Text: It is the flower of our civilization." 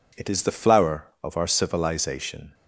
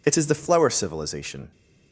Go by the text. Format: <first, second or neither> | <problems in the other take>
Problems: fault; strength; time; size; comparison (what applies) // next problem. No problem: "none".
first | skips "of our"; at 0.6 s